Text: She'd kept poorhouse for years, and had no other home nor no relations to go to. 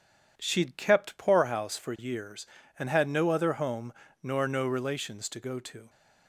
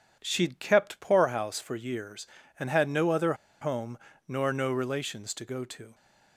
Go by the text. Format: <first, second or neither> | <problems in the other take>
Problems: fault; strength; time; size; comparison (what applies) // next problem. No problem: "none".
first | pauses between "other" and "home"; slight; at 3.3 s; 0.27 s long // pauses between "home" and "nor"; slight; at 3.9 s; 0.30 s long; slight in the first